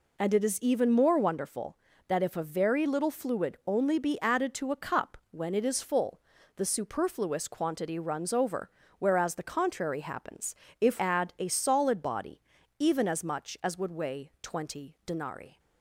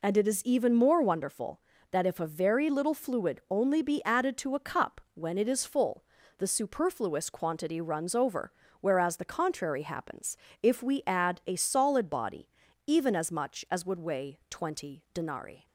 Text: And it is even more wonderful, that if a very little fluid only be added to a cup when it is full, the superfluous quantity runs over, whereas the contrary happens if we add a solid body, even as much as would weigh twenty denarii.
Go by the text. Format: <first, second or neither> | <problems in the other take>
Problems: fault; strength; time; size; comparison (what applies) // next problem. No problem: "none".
second | pauses between "happens" and "if"; slight; at 10.5 s; 0.24 s long; slight in the second // skips "we"; at 10.9 s